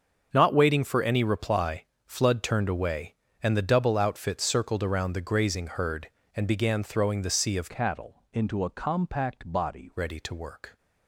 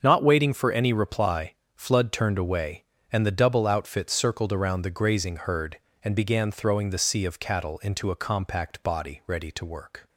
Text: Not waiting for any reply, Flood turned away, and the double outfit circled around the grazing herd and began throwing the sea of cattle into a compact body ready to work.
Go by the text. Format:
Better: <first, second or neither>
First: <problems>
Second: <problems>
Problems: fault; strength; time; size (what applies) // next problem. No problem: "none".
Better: second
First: starts louder than the rest; until 1.3 s; 7 dB // changes voice from "cattle" to "body"; from 7.6 to 9.8 s; 2.2 s long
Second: starts louder than the rest; until 1.0 s; 7 dB